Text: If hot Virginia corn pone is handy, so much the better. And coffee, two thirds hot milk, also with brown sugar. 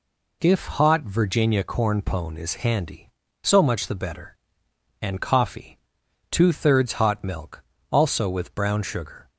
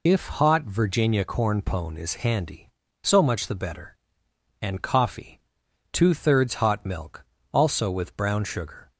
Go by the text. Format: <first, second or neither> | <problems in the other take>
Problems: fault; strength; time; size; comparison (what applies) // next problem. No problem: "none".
first | loses the start of "If"; at 0.0 s; 35 ms